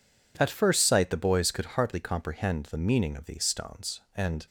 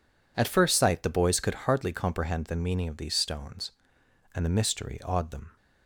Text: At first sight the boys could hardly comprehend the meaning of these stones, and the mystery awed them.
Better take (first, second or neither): second